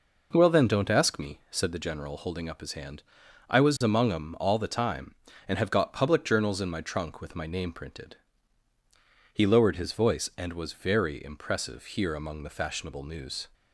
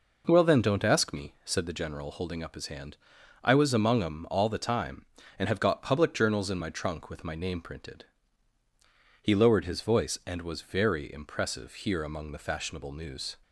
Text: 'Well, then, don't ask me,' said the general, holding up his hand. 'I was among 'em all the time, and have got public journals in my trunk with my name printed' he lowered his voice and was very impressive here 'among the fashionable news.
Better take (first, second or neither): neither